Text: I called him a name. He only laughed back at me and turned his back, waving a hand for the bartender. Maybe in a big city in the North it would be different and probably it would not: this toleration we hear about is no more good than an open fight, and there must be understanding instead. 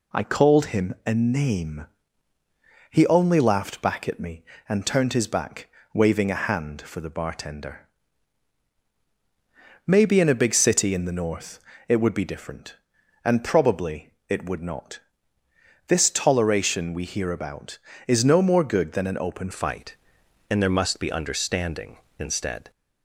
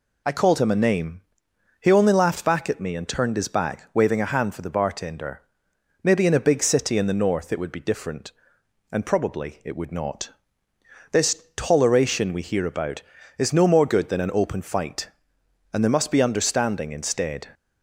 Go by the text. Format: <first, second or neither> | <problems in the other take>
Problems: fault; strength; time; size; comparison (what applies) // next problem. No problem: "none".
second | pauses between "North" and "it"; slight; at 11.5 s; 0.28 s long // pauses between "probably" and "it"; slight; at 14.1 s; 0.18 s long // changes voice at "fight"; from 19.5 s on; 3.2 s long